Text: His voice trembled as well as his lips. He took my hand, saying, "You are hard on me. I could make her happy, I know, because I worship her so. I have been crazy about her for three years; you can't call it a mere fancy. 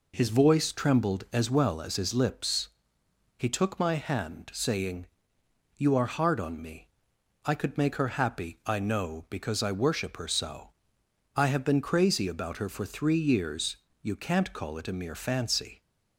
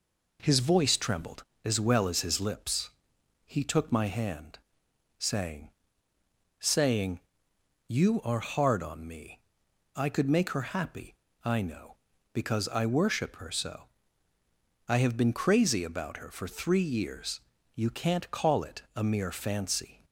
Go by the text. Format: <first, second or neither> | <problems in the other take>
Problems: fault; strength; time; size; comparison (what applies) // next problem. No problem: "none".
first | says "saying" twice; at 6.6 s